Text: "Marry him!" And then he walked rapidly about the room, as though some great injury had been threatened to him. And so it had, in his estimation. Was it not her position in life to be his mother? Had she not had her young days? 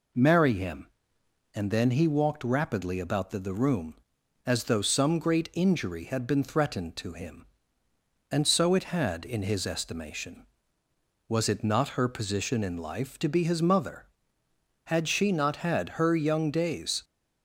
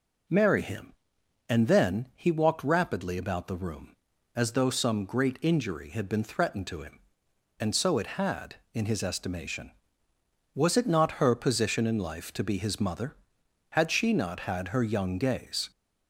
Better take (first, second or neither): second